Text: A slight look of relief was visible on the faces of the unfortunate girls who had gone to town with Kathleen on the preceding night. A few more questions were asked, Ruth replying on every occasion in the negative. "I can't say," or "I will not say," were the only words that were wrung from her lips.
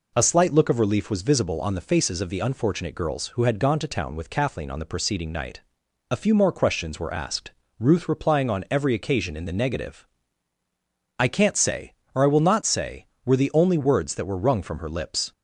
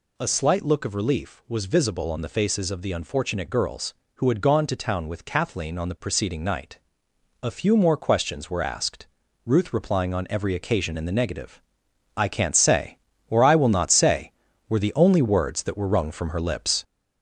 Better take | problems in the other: first | gets louder; noticeable; throughout; 4.5 dB

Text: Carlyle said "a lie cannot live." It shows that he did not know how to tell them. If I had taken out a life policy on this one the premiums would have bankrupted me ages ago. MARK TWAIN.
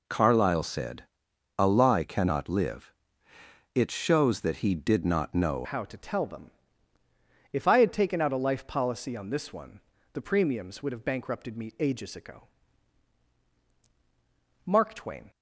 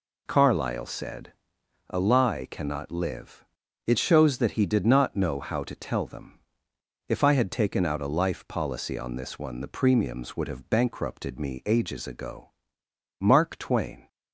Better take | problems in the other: second | pauses between "said" and "a"; noticeable; at 1.0 s; 0.52 s long; noticeable in the second // changes voice at "how"; from 5.6 s on; 9.6 s long // pauses between "one" and "the"; slight; at 9.7 s; 0.32 s long

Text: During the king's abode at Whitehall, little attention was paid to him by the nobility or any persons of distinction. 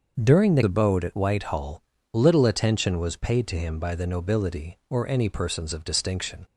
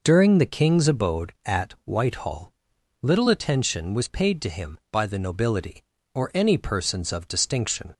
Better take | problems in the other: second | starts louder than the rest; until 1.2 s; 6.5 dB // skips "king's"; at 0.6 s

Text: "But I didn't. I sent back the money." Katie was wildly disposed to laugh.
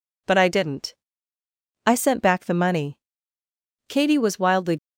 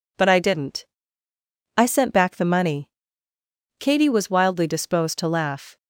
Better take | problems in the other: second | stops before "disposed to laugh"; at 4.7 s

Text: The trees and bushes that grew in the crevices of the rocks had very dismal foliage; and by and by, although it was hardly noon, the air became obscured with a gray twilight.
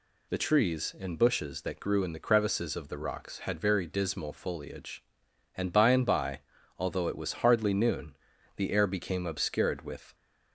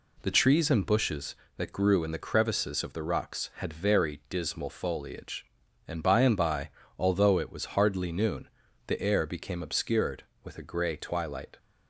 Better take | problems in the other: second | stops before "a gray twilight"; at 10.1 s

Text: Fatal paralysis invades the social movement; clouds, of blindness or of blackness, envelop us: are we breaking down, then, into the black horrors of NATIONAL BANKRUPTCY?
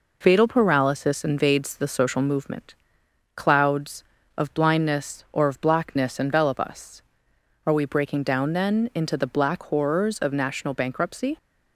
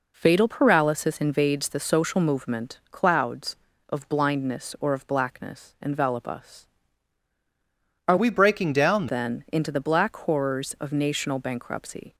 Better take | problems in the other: first | changes voice from "we" to "down"; from 8.1 to 9.0 s; 0.9 s long

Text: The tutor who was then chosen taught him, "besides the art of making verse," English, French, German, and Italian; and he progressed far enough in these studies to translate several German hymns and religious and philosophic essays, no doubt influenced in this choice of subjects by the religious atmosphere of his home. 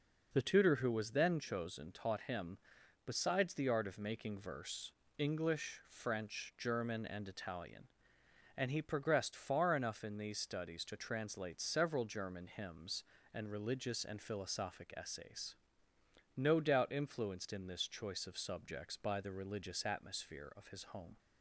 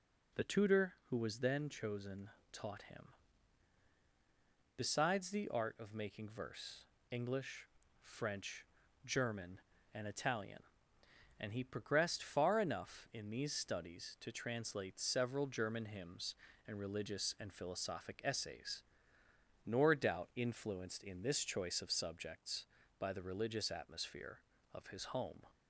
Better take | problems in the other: first | pauses between "chosen" and "taught"; slight; at 2.3 s; 0.20 s long // says "nor" for "no"; at 19.6 s

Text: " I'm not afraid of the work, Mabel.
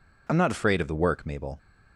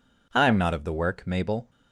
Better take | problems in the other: first | skips "afraid"; at 0.7 s

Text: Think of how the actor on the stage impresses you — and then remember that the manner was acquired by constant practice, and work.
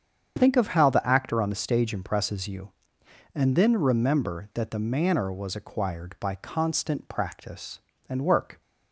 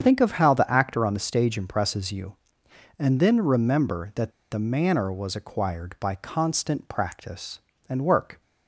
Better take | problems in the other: first | starts louder than the rest; strong; until 1.0 s; 7.5 dB; strong in the first // pauses between "that" and "the"; slight; at 4.3 s; 0.20 s long

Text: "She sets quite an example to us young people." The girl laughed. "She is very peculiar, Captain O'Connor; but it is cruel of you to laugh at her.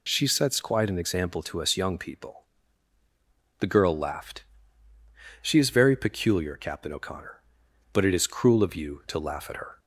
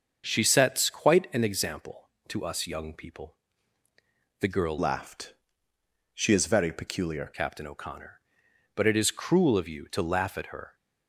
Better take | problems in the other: first | starts louder than the rest; until 1.2 s; 6.5 dB // changes voice from "laughed" to "peculiar"; from 4.7 to 7.2 s; 2.5 s long

